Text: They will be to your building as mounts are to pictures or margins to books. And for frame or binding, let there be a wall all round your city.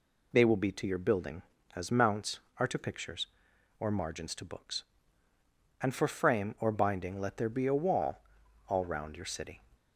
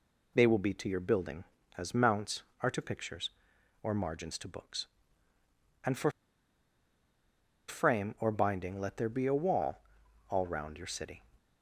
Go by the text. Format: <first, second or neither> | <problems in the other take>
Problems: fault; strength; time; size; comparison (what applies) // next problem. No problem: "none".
first | pauses between "for" and "frame"; strong; at 6.1 s; 1.5 s long // pauses between "wall" and "all"; noticeable; at 9.7 s; 0.50 s long; noticeable in the first